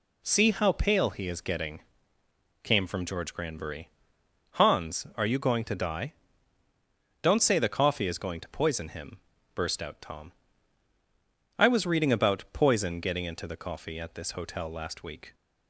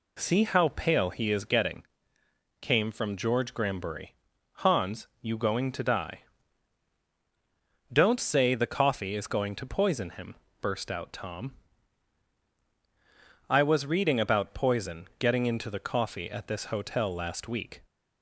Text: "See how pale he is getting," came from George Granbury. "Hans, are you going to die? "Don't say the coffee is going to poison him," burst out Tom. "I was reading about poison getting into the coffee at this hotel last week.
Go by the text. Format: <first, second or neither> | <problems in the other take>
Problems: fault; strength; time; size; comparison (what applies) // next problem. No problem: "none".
first | skips "are"; at 5.1 s